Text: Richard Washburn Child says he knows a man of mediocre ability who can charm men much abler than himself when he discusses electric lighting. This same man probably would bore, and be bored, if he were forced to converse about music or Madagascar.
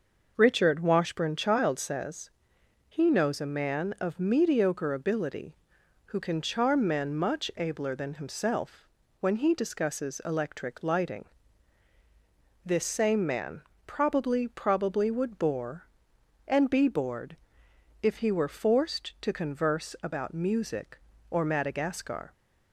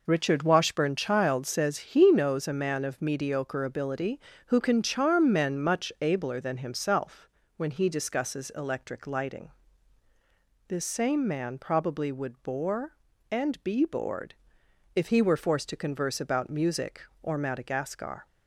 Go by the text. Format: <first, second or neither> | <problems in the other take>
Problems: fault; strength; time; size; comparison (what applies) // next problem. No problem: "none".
second | pauses between "says" and "he"; noticeable; at 2.2 s; 0.60 s long // pauses between "himself" and "when"; slight; at 8.8 s; 0.32 s long; slight in the second // pauses between "man" and "probably"; slight; at 13.6 s; 0.24 s long // says "probably" twice; at 14.4 s